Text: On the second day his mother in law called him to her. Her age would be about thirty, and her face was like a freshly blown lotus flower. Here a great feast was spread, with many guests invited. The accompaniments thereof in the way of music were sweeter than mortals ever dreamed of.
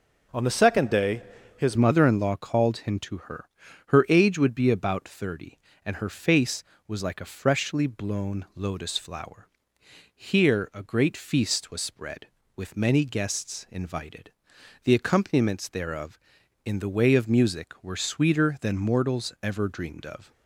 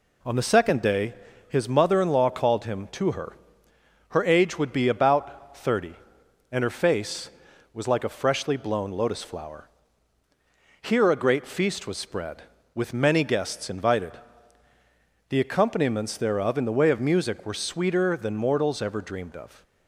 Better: second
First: pauses between "day" and "his"; slight; at 1.2 s; 0.34 s long // changes voice at "mother"; from 1.7 s on; 18.6 s long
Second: pauses between "day" and "his"; slight; at 1.1 s; 0.34 s long

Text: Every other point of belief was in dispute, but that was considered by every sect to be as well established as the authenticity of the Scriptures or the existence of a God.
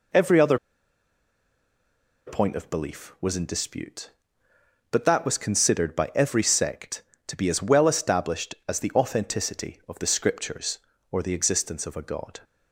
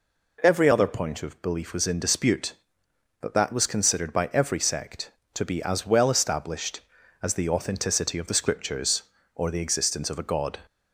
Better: second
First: pauses between "other" and "point"; strong; at 0.5 s; 1.6 s long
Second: none

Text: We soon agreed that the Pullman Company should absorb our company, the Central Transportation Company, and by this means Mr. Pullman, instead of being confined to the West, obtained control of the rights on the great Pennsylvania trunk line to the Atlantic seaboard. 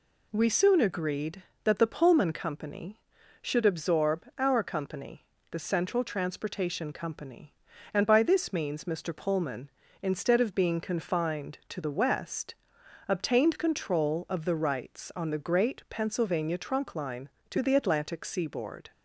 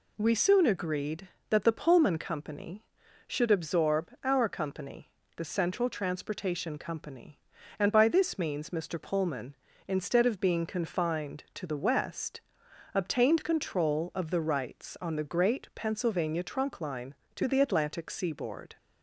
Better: neither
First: none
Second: none

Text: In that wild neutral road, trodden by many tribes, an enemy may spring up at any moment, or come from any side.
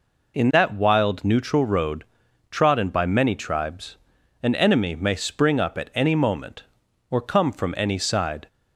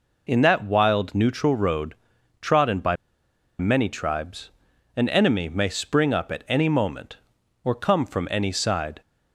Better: first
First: none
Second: pauses between "by" and "many"; noticeable; at 2.9 s; 0.65 s long

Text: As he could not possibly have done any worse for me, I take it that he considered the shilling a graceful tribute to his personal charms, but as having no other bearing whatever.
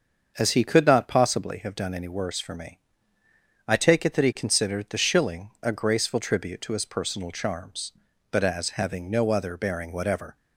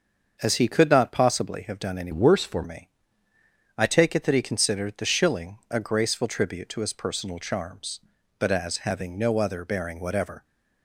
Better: first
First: starts louder than the rest; until 1.3 s; 7 dB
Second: starts louder than the rest; until 1.4 s; 6.5 dB // changes voice from "worse" to "for"; from 2.1 to 2.6 s; 0.5 s long

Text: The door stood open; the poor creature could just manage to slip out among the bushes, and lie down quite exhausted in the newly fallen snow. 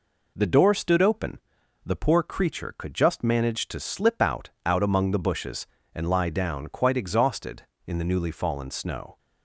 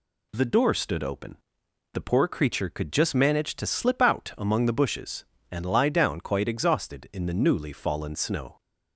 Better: second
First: says "out" twice; at 4.6 s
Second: none

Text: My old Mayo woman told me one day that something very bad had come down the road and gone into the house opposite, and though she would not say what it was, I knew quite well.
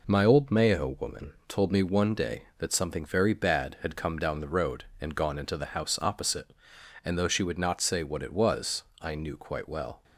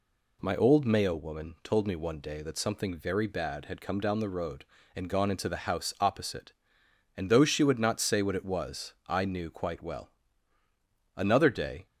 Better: first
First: none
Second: goes on to say "Another day"; noticeable; from 11.1 s on; 0.70 s long

